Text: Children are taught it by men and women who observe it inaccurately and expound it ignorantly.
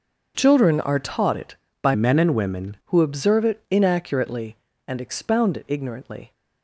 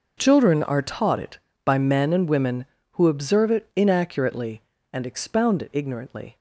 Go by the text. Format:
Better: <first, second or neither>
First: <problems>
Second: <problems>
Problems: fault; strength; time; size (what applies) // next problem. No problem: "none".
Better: second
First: changes voice from "men" to "women"; from 1.9 to 2.7 s; 0.8 s long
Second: none